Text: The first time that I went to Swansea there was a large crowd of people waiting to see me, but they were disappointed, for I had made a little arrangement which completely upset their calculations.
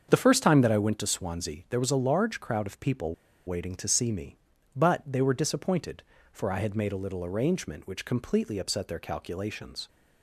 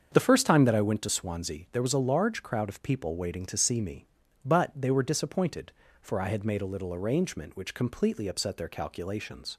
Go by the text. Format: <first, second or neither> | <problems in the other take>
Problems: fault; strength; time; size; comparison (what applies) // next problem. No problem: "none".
second | starts louder than the rest; strong; until 1.1 s; 7 dB; strong in the second // pauses between "people" and "waiting"; slight; at 3.1 s; 0.33 s long